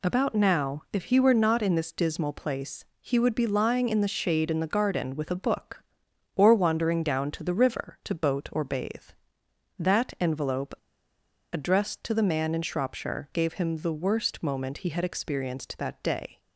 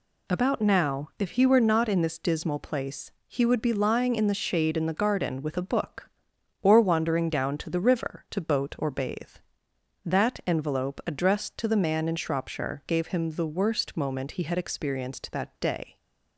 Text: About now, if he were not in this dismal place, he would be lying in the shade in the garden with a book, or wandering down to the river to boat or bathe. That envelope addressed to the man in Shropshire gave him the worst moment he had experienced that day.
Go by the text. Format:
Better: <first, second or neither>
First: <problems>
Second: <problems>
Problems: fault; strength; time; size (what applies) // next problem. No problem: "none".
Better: second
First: pauses between "envelope" and "addressed"; noticeable; at 10.7 s; 0.77 s long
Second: none